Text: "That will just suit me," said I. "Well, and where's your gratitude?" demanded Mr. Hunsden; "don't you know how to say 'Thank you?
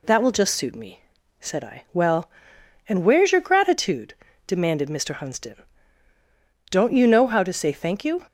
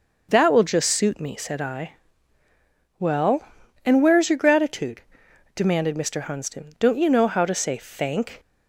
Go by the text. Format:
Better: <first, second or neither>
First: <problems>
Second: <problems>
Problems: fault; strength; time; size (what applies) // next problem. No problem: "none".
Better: first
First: none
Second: stops before "you"; at 8.3 s